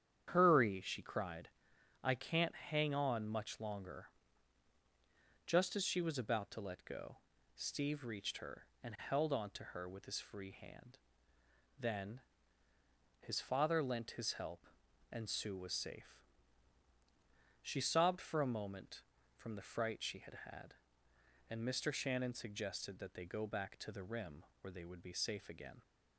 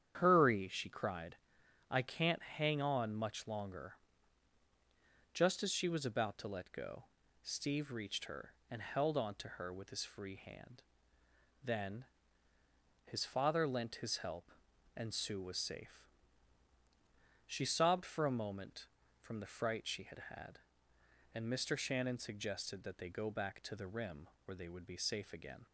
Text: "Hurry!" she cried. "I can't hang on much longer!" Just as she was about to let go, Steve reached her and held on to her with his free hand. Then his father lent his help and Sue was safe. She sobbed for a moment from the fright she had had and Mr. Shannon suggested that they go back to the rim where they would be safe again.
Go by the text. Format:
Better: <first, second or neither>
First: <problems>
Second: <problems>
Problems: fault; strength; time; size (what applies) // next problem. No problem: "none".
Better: neither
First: starts louder than the rest; strong; until 1.3 s; 9 dB // pauses between "Then" and "his"; noticeable; at 12.2 s; 0.98 s long // pauses between "rim" and "where"; slight; at 24.4 s; 0.16 s long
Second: starts louder than the rest; strong; until 1.2 s; 9 dB // pauses between "Then" and "his"; noticeable; at 12.0 s; 0.98 s long // pauses between "rim" and "where"; slight; at 24.2 s; 0.16 s long